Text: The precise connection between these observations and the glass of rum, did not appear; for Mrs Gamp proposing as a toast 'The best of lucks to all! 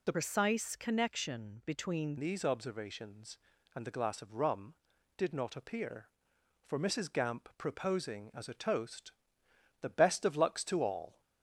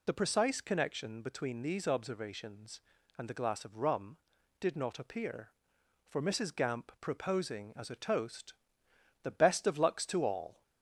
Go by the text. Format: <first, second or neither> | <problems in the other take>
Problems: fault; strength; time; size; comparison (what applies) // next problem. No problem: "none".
second | changes voice from "precise" to "between"; from 0.1 to 2.1 s; 2.0 s long // pauses between "toast" and "The"; noticeable; at 9.1 s; 0.70 s long; noticeable in the second